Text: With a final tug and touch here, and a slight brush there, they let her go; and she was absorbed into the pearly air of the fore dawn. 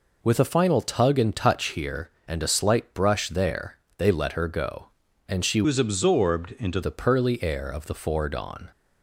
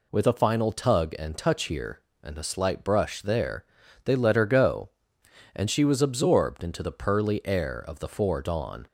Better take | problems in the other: second | changes voice from "was" to "into"; from 5.6 to 6.8 s; 1.2 s long

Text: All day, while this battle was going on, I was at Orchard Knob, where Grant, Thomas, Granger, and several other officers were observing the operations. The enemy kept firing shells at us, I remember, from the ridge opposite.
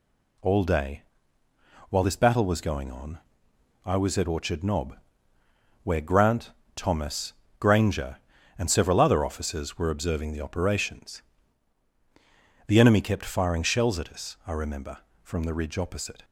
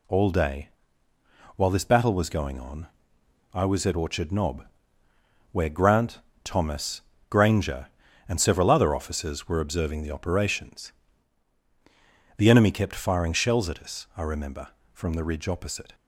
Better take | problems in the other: neither | none

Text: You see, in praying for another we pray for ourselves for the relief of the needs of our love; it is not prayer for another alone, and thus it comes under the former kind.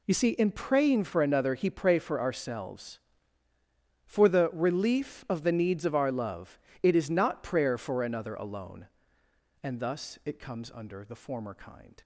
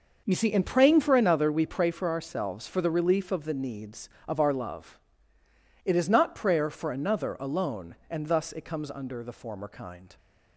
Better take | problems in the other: second | says "he" for "we"; at 1.5 s

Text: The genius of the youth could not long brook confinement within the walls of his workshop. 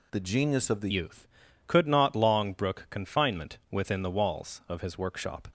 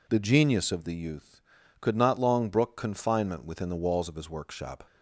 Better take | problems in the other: second | changes voice at "youth"; from 0.9 s on; 4.5 s long

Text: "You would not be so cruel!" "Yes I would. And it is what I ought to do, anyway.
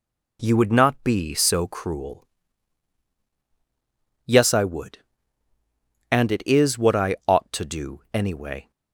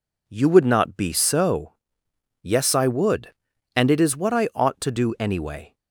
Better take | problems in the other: first | skips "cruel"; at 2.0 s

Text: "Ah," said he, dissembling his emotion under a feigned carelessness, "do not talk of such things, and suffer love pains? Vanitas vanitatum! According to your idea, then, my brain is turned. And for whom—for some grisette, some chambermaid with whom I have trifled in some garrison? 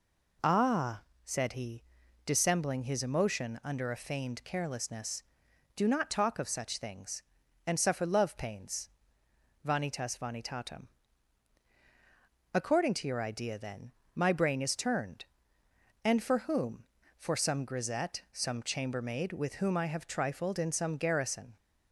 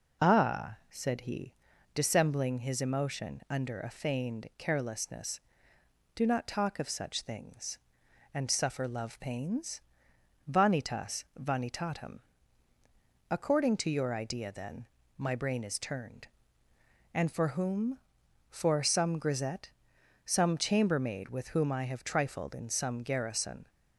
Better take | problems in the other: neither | none

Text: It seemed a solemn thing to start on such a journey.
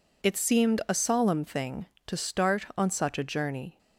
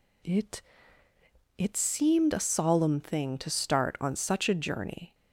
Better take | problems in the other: first | says "It" twice; at 1.5 s

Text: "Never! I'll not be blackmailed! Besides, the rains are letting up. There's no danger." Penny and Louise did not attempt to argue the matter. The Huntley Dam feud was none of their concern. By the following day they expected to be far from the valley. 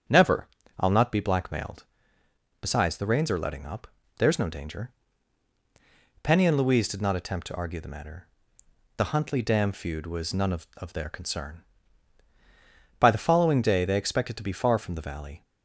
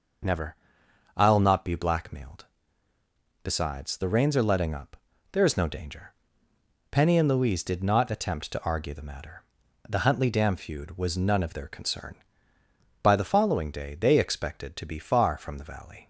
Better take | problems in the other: second | starts louder than the rest; strong; until 1.4 s; 8 dB // says "of" twice; at 10.7 s

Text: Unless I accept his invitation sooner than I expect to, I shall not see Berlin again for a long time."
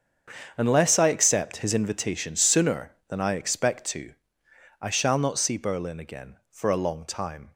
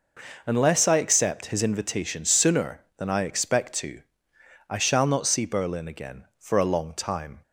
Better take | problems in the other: second | gets quieter; strong; throughout; 14.5 dB

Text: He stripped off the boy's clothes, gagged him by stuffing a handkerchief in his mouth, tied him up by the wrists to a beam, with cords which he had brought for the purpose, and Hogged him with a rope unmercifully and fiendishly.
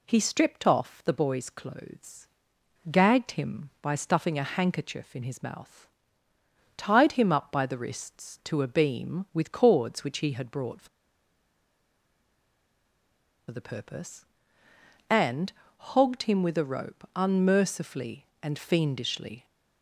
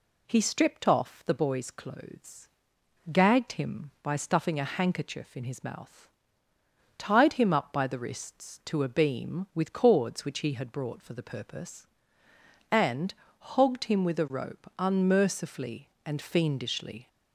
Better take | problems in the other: second | pauses between "for" and "the"; strong; at 10.8 s; 2.6 s long // pauses between "and" and "Hogged"; slight; at 15.5 s; 0.24 s long; slight in the second

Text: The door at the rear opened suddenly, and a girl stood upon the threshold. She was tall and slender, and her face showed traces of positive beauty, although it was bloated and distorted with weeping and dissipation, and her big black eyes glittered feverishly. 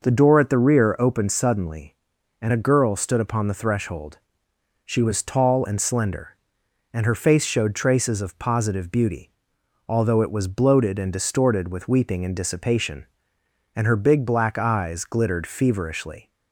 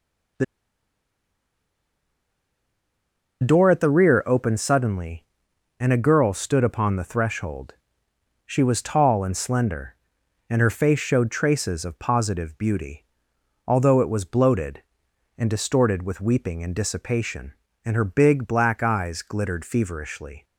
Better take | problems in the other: first | pauses between "The" and "door"; strong; at 0.4 s; 2.9 s long

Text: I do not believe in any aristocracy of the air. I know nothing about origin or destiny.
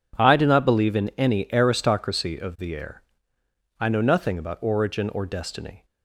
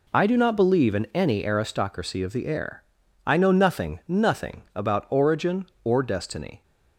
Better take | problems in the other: first | says "nothing" twice; at 4.0 s

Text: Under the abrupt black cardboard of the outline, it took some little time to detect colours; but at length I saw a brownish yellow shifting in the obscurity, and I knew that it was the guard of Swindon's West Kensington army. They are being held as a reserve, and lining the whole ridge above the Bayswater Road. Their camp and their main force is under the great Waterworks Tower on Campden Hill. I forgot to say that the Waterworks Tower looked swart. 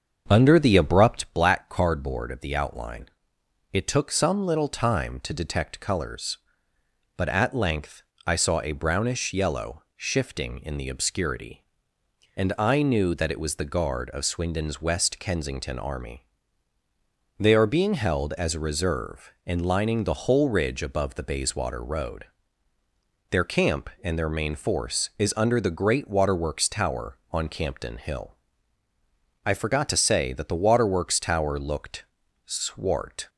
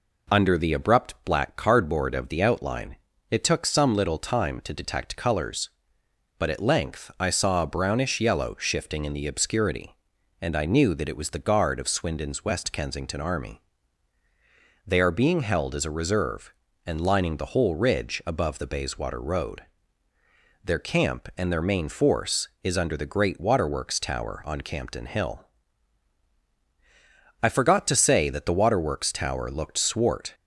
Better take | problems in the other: second | starts louder than the rest; until 1.3 s; 7 dB // pauses between "length" and "I"; slight; at 8.0 s; 0.22 s long // pauses between "looked" and "swart"; at 32.0 s; 0.42 s long

